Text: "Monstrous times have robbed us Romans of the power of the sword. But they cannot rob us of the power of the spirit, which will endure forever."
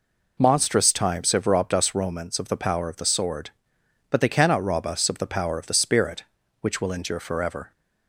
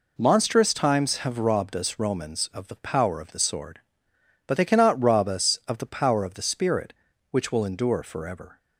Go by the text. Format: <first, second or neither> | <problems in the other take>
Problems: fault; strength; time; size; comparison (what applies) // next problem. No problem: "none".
neither | none